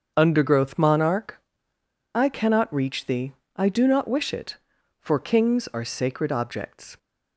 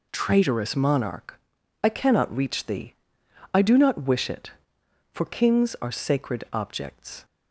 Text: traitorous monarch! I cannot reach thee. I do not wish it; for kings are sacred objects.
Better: second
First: starts louder than the rest; until 1.1 s; 6.5 dB // says "undergrowth" for "traitorous"; at 0.1 s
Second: none

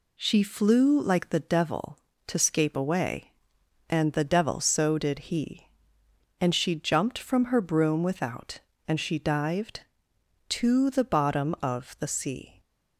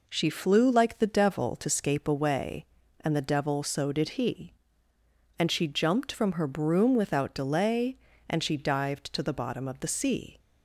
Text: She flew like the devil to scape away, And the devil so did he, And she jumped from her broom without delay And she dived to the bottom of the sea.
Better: second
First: skips "delay"; at 8.7 s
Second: none

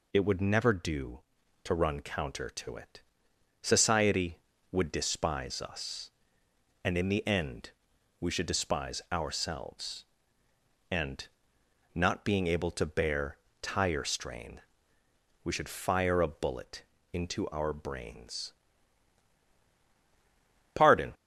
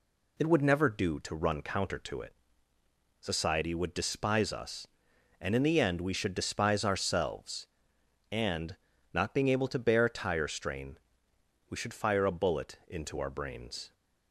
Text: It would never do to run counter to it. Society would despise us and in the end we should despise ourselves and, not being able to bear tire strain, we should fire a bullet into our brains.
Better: second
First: pauses between "end" and "we"; noticeable; at 7.6 s; 0.50 s long // pauses between "bear" and "tire"; slight; at 13.3 s; 0.24 s long // pauses between "bullet" and "into"; slight; at 16.8 s; 0.30 s long // goes on to say "Pardon"; slight; from 20.7 s on; 0.38 s long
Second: none

